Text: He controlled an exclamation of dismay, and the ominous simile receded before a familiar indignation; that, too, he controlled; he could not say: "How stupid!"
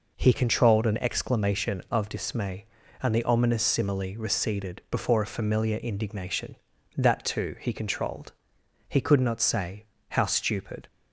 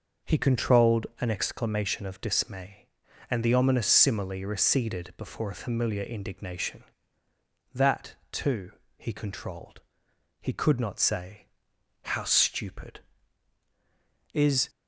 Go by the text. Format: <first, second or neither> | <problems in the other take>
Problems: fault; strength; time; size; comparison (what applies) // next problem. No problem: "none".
first | goes on to say "Is"; slight; from 14.3 s on; 0.38 s long